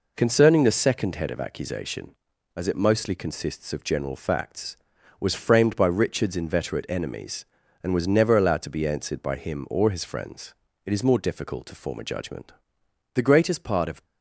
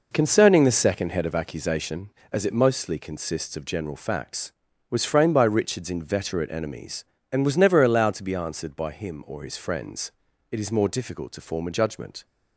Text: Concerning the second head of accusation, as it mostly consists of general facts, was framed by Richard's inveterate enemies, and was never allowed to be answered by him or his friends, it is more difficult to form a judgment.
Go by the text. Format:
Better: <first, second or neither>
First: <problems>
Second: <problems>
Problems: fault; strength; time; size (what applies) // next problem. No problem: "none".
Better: second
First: goes on to say "The greatest part of"; noticeable; from 13.1 s on; 0.92 s long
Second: none